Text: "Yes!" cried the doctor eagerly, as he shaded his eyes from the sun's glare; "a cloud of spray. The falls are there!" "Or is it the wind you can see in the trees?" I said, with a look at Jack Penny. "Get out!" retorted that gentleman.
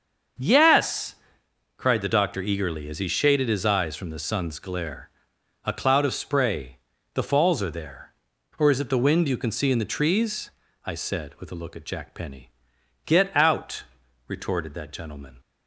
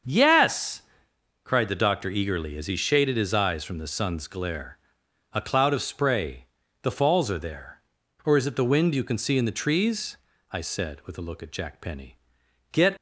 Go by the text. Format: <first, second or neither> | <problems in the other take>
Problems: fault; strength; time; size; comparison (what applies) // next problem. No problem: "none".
first | starts louder than the rest; until 1.7 s; 6.5 dB; also in the first // stops before "out retorted that gentleman"; at 12.9 s